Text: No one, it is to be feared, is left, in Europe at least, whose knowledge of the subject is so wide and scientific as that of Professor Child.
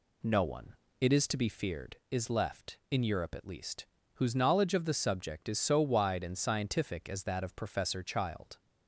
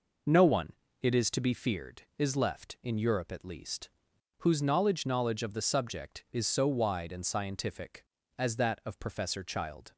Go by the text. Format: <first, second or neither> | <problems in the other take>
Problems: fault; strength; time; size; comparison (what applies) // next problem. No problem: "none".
first | says "knowledge" twice; at 5.0 s